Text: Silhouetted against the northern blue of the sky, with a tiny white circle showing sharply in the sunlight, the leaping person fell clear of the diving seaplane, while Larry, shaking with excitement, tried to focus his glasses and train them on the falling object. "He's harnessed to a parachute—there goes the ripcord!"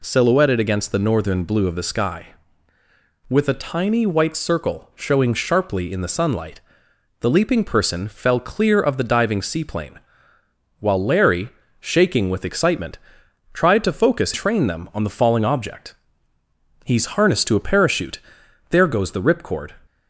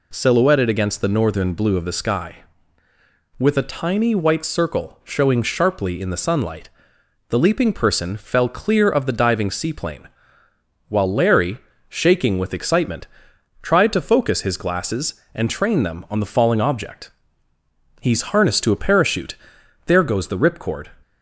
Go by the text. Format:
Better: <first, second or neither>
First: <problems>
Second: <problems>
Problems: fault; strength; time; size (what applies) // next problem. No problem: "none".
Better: second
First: skips "his glasses and"; at 14.3 s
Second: none